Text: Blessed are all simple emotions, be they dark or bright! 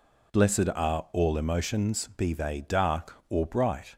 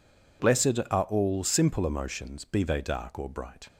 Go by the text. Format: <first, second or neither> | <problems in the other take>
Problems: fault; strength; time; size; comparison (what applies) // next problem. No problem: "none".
second | skips "simple"; at 1.3 s